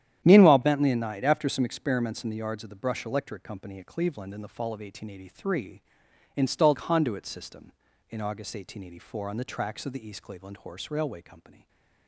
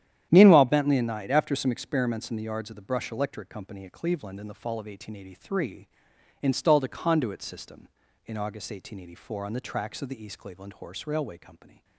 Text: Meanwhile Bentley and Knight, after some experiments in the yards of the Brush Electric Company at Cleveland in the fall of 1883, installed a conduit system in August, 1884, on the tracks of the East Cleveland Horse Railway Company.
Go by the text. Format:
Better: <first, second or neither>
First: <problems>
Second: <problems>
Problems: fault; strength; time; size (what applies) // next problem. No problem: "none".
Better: second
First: starts louder than the rest; strong; until 1.2 s; 10.5 dB // skips "a"; at 6.7 s // stays silent after the last word; slight; from 11.5 s on; 0.5 s long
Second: starts louder than the rest; strong; until 1.3 s; 10.5 dB